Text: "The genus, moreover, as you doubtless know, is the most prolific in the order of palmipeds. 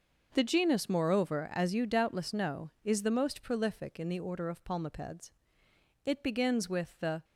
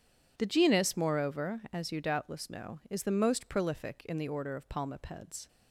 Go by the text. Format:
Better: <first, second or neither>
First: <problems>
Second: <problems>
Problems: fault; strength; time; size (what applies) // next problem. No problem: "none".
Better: second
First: goes on to say "It begins with the"; noticeable; from 6.0 s on; 1.2 s long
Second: none